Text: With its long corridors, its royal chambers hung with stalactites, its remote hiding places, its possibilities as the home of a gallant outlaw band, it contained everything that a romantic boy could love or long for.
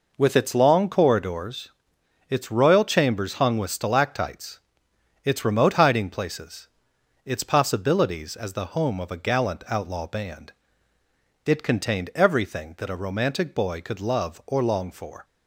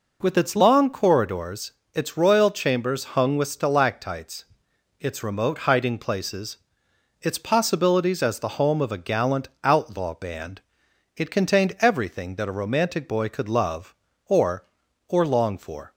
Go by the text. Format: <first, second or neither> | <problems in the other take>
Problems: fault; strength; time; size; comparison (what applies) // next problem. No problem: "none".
first | pauses between "gallant" and "outlaw"; slight; at 9.4 s; 0.16 s long // says "or" twice; at 15.0 s